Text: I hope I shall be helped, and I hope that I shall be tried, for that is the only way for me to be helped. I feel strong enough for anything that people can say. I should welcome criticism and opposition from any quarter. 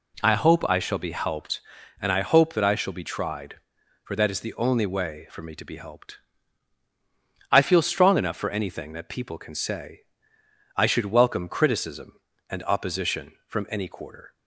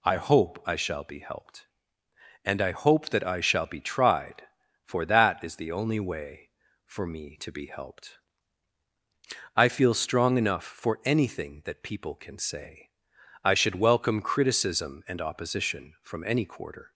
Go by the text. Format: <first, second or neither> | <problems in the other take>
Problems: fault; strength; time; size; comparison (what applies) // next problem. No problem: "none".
neither | none